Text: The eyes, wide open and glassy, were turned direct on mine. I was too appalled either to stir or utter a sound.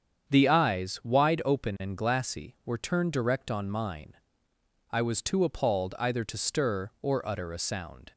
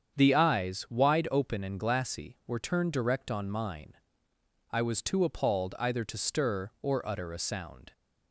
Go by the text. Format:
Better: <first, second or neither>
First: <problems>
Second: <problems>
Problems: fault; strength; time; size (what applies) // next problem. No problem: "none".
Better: neither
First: starts louder than the rest; strong; until 1.3 s; 7.5 dB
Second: starts louder than the rest; strong; until 1.2 s; 8 dB